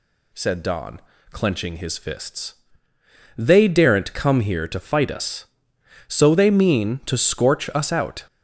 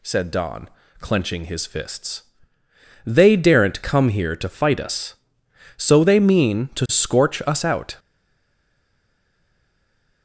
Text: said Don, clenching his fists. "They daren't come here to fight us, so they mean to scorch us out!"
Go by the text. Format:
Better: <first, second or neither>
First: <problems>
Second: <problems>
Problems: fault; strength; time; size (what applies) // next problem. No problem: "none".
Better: first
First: none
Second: stays silent after the last word; from 7.9 s on; 2.3 s long